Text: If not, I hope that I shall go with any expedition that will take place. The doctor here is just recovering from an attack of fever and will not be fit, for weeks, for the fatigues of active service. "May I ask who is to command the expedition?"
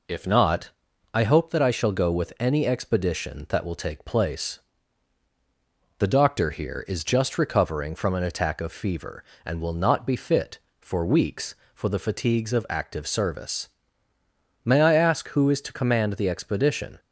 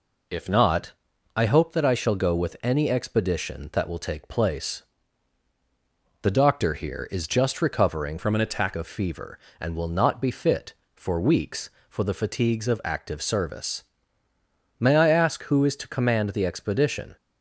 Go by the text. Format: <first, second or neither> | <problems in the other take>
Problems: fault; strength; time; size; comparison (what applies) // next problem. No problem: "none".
first | changes voice from "from" to "attack"; from 8.1 to 8.7 s; 0.6 s long